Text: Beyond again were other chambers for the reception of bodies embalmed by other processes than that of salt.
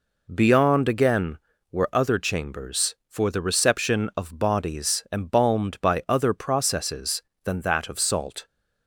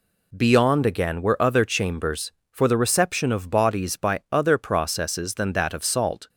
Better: first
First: none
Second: skips "embalmed"; at 3.9 s

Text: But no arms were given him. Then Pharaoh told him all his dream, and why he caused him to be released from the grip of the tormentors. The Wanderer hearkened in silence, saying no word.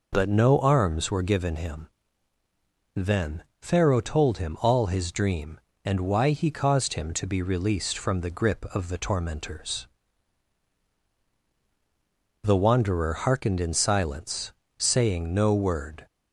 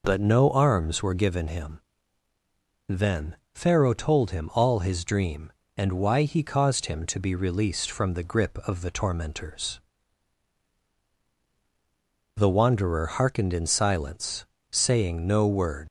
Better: first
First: pauses between "Then" and "Pharaoh"; slight; at 3.4 s; 0.18 s long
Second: pauses between "Then" and "Pharaoh"; slight; at 3.3 s; 0.18 s long // leaves "word" unfinished; at 15.8 s; 105 ms

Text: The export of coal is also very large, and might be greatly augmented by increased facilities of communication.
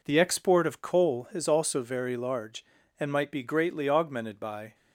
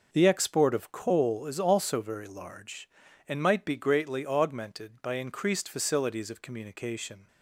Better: second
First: stops before "increased facilities of communication"; at 4.7 s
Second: none

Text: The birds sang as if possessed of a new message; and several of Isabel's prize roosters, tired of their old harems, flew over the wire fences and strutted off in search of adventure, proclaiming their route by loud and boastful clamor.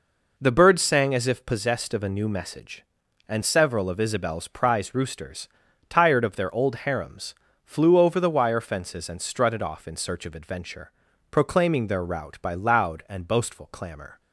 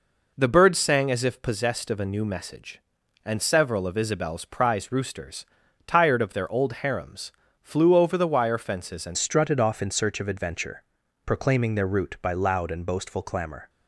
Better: first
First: none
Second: changes voice at "strutted"; from 9.1 s on; 4.5 s long

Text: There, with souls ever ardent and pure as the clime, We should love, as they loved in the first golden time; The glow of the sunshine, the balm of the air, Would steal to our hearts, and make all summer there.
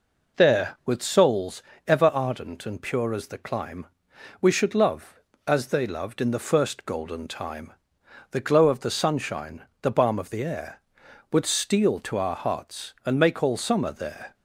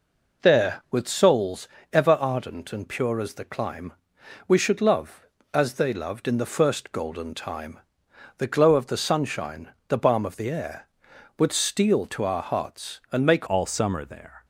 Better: first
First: pauses between "souls" and "ever"; slight; at 1.6 s; 0.24 s long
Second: pauses between "souls" and "ever"; slight; at 1.6 s; 0.24 s long // changes voice at "all"; from 13.4 s on; 1.0 s long

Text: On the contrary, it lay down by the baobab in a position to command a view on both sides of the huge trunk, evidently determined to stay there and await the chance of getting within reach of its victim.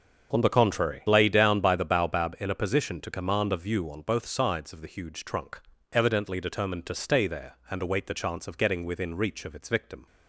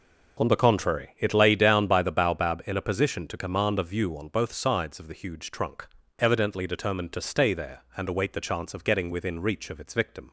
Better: second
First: starts louder than the rest; strong; until 1.4 s; 7 dB // skips "it"; at 1.0 s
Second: starts louder than the rest; until 1.5 s; 6 dB

